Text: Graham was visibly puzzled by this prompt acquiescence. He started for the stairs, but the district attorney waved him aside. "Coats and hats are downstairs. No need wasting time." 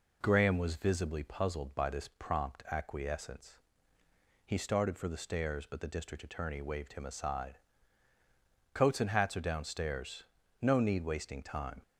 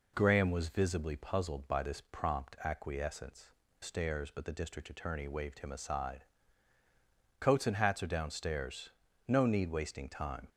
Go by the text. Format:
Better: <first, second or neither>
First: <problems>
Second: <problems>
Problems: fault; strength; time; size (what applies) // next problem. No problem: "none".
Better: first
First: none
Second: skips "He started for the"; at 3.6 s